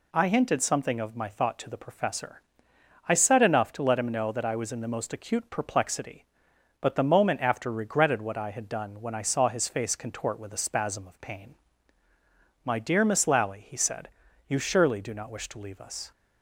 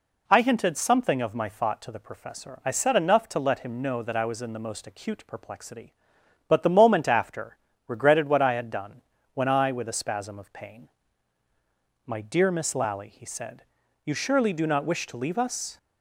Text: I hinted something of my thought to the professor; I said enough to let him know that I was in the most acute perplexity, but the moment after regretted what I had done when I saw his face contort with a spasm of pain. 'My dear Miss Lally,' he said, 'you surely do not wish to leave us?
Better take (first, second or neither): first